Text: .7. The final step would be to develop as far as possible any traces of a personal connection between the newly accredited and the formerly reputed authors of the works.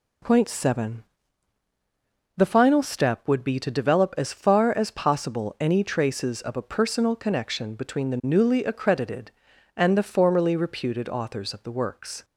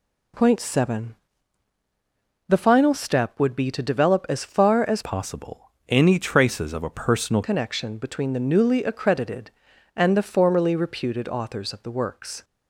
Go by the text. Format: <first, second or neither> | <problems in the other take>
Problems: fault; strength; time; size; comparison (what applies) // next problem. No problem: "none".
first | changes voice from "possible" to "personal"; from 5.0 to 7.4 s; 2.4 s long // pauses between "possible" and "any"; slight; at 5.6 s; 0.20 s long